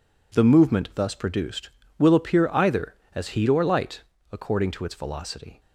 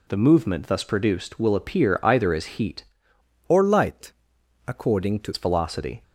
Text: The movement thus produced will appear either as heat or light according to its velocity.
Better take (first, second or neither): first